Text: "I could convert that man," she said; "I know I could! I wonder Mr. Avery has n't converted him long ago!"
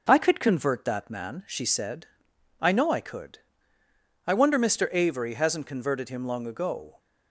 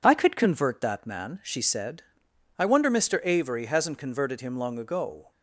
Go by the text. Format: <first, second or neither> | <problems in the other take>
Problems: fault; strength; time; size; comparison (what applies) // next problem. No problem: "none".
first | skips "I know I could"; at 2.2 s